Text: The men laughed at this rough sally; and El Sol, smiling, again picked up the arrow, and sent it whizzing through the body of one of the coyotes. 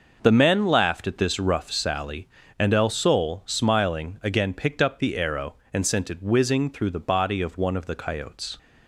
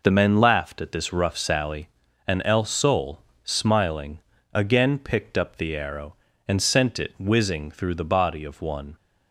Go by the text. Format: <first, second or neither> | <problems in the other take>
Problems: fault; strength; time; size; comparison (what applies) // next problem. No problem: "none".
first | stops before "of the coyotes"; at 8.9 s